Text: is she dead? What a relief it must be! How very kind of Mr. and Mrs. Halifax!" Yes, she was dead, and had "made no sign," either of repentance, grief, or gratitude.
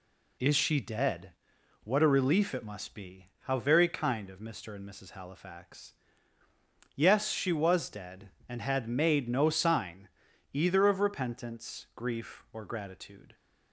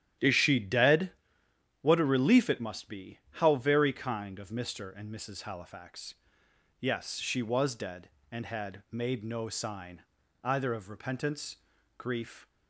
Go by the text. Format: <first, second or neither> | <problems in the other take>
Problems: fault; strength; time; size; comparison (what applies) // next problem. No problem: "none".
first | starts louder than the rest; strong; until 1.9 s; 11.5 dB // stops before "or gratitude"; at 12.4 s